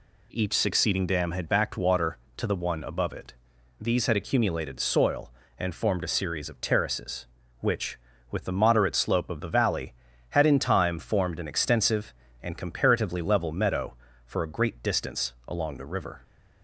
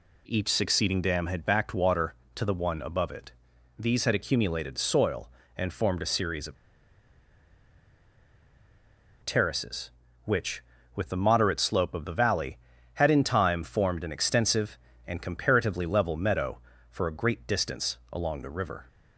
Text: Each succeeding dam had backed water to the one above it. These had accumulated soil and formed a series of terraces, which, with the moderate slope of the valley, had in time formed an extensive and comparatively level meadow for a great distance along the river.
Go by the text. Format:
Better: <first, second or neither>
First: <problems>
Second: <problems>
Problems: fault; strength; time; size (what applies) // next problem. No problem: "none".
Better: first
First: none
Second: pauses between "of" and "terraces"; strong; at 6.5 s; 2.6 s long